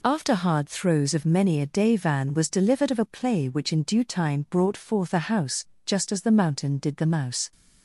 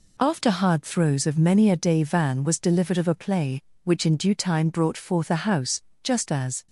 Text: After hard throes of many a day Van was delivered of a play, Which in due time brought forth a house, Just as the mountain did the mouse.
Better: first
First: none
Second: stops before "the mountain did the mouse"; at 6.6 s

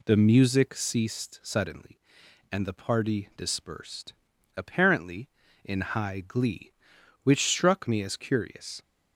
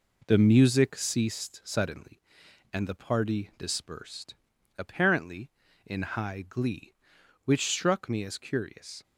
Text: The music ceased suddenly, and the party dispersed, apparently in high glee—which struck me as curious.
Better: first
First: none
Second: gets quieter; noticeable; throughout; 5.5 dB

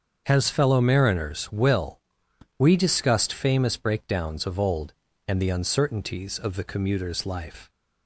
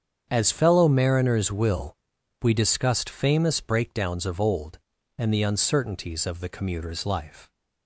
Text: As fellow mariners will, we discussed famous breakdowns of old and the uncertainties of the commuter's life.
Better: second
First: starts louder than the rest; until 1.2 s; 7 dB // says "Has" for "As"; at 0.2 s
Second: starts louder than the rest; strong; until 1.3 s; 7.5 dB

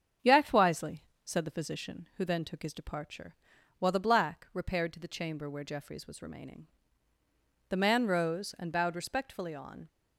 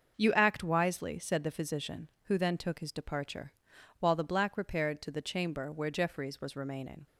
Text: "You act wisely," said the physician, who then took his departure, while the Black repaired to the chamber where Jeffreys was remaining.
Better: second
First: starts louder than the rest; strong; until 1.4 s; 7.5 dB // goes on to say "The man rose and bowed respectfully on"; strong; from 7.6 s on; 2.1 s long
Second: starts louder than the rest; until 1.1 s; 6.5 dB

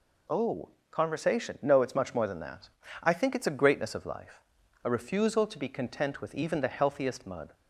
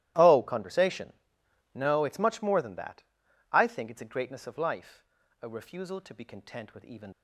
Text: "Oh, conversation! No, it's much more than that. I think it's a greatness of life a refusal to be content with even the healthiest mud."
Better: first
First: pauses between "life" and "a"; at 4.4 s; 0.42 s long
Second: starts louder than the rest; strong; until 1.8 s; 15 dB // pauses between "life" and "a"; at 5.0 s; 0.38 s long // stops before "the healthiest mud"; at 7.1 s

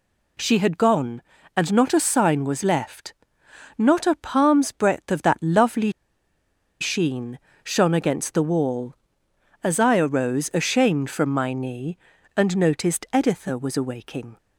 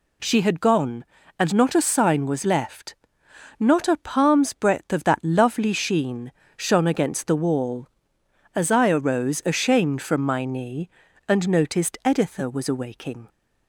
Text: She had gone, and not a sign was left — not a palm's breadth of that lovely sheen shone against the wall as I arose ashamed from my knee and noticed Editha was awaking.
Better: second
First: pauses between "lovely" and "sheen"; noticeable; at 5.9 s; 0.90 s long // pauses between "sheen" and "shone"; slight; at 7.3 s; 0.26 s long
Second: pauses between "sheen" and "shone"; slight; at 6.3 s; 0.26 s long

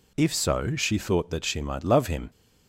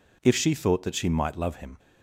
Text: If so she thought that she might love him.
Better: first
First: none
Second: skips "so"; at 0.3 s

